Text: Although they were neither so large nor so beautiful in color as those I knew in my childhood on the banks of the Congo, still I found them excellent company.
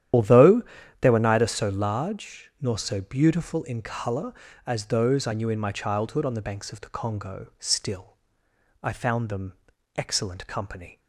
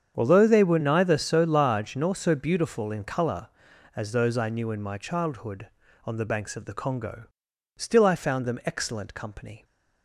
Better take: second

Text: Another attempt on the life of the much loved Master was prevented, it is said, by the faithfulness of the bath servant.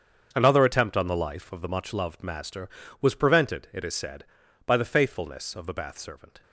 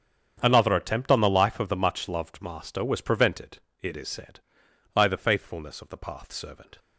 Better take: first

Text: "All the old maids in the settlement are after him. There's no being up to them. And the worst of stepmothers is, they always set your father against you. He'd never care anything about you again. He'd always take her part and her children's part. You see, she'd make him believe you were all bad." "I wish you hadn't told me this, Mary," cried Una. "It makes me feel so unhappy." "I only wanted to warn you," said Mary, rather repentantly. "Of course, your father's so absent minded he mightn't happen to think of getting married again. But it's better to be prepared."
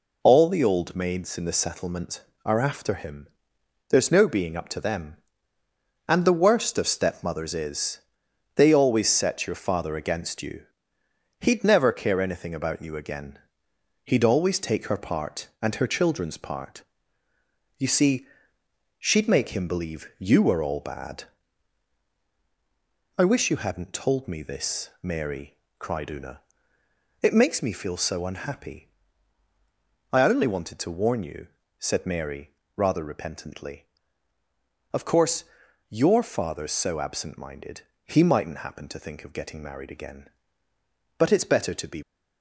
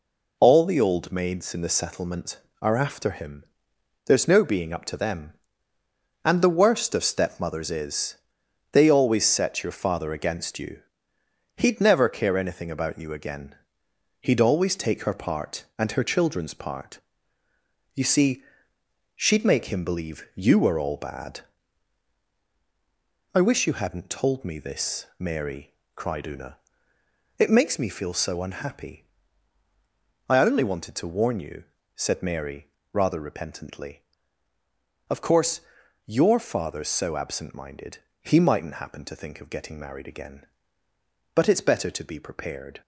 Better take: second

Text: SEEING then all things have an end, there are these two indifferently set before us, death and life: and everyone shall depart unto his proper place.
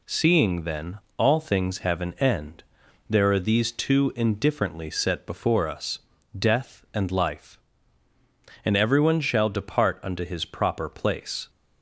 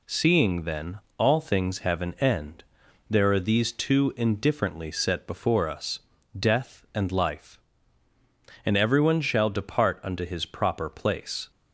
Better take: neither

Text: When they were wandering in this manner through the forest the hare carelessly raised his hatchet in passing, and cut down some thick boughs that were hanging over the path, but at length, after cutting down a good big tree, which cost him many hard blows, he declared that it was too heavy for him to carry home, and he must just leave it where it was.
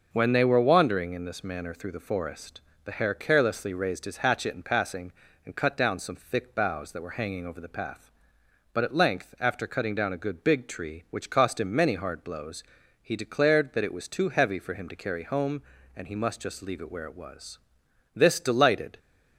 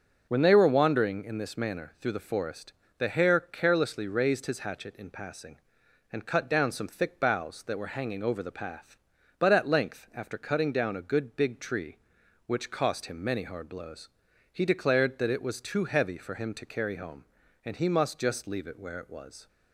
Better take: second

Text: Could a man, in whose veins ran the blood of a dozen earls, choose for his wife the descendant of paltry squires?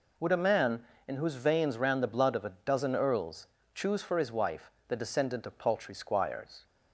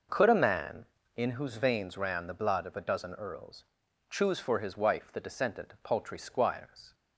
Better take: second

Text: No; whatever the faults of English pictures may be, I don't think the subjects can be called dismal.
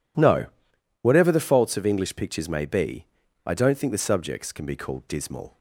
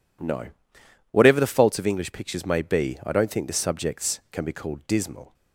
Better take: neither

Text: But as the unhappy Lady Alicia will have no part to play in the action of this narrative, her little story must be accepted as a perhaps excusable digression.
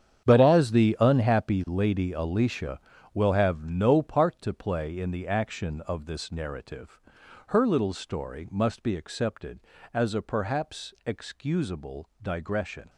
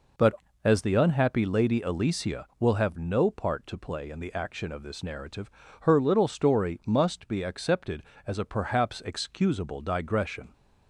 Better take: second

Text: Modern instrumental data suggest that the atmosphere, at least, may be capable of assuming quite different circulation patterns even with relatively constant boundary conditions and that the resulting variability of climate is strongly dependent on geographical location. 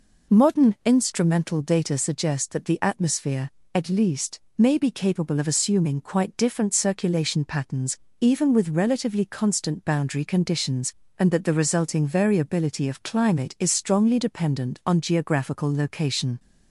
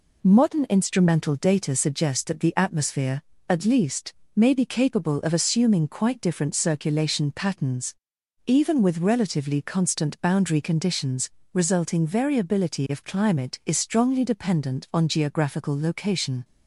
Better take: first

